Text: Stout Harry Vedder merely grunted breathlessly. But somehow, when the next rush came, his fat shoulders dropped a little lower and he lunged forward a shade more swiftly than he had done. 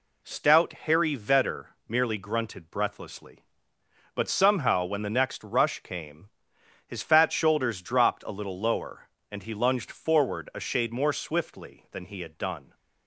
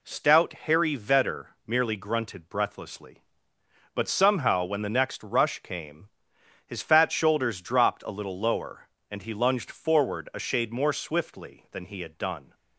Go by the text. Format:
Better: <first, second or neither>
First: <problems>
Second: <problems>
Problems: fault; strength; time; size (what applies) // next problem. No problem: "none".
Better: neither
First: pauses between "Vedder" and "merely"; slight; at 1.7 s; 0.18 s long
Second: pauses between "Vedder" and "merely"; slight; at 1.5 s; 0.16 s long